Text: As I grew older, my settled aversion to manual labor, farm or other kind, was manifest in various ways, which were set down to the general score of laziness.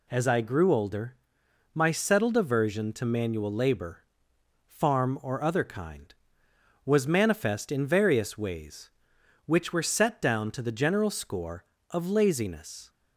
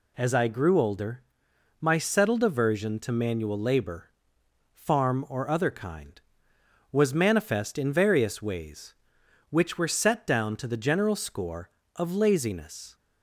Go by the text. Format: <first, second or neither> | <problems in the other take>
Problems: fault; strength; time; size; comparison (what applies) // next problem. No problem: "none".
neither | none